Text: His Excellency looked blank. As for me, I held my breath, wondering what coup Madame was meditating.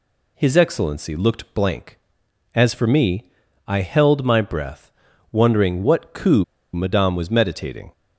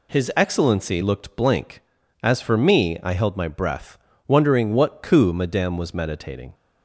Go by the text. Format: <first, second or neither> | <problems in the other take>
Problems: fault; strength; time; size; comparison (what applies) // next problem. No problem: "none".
second | pauses between "coup" and "Madame"; slight; at 6.4 s; 0.29 s long